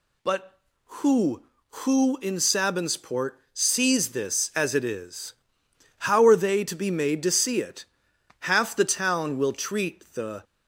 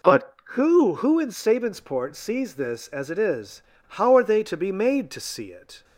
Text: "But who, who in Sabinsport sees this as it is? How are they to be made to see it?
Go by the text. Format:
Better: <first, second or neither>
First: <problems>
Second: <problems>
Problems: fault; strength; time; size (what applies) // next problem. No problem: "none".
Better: second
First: pauses between "Sabinsport" and "sees"; slight; at 3.3 s; 0.16 s long // goes on to say "Half the town will treat the"; strong; from 8.3 s on; 2.0 s long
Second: none